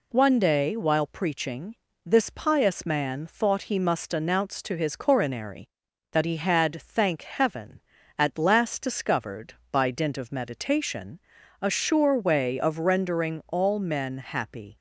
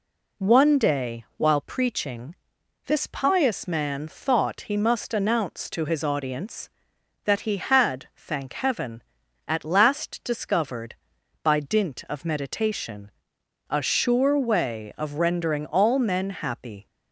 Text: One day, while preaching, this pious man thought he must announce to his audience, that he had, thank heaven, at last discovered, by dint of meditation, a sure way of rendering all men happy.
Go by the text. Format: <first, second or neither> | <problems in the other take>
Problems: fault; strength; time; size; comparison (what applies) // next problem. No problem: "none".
second | says "coronary" for "audience"; at 4.9 s